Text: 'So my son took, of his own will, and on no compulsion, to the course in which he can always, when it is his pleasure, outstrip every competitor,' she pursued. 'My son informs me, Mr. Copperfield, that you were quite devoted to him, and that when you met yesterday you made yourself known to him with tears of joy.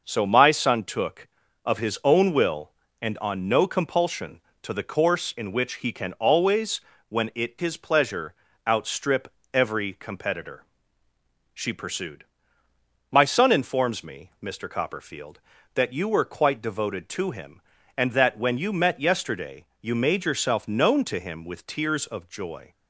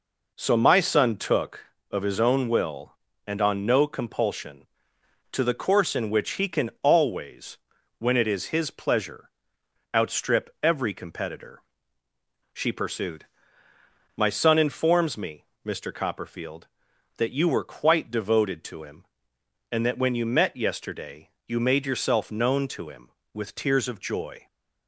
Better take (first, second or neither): second